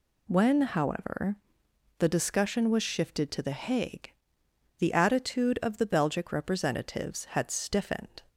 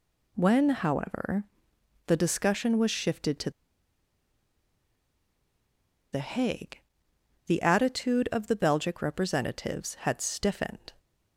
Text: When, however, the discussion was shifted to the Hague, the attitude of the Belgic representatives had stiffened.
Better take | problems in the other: first | pauses between "to" and "the"; strong; at 3.4 s; 2.6 s long

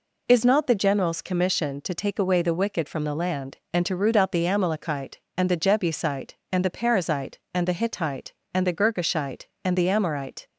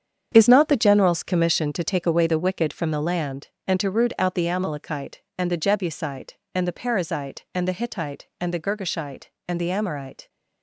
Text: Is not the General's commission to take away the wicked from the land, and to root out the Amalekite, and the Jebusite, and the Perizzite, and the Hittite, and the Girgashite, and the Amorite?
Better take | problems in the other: first | gets quieter; strong; throughout; 10 dB

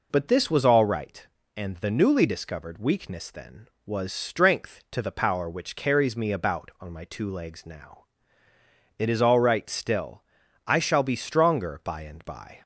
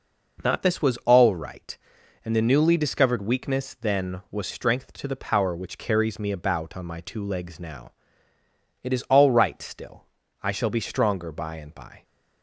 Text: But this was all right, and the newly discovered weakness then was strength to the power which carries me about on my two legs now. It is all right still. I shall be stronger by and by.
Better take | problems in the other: first | says "Not" for "But"; at 0.4 s

